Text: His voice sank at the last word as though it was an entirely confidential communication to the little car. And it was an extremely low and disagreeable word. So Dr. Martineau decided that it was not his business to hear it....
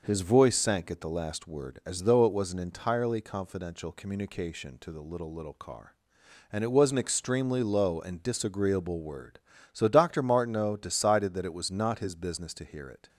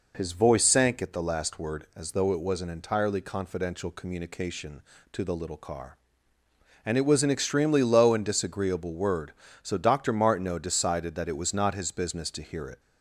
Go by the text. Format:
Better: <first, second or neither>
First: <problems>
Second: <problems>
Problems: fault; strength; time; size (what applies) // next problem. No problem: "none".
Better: second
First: says "little" twice; at 5.3 s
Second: none